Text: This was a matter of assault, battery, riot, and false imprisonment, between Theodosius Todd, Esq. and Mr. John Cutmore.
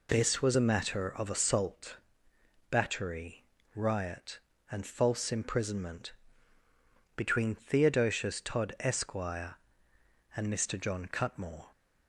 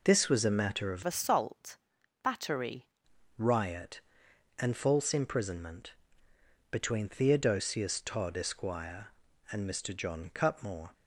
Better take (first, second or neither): first